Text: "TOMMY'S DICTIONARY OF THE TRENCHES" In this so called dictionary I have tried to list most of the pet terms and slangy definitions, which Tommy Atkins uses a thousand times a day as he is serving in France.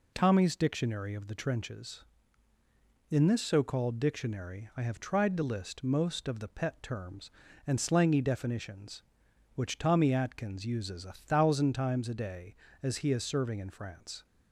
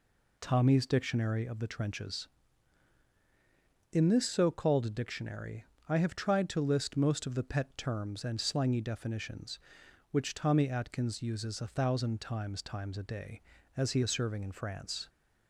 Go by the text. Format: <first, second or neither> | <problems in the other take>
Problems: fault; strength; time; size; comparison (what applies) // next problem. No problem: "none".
first | pauses between "dictionary" and "I"; slight; at 5.6 s; 0.26 s long // says "times" twice; at 12.6 s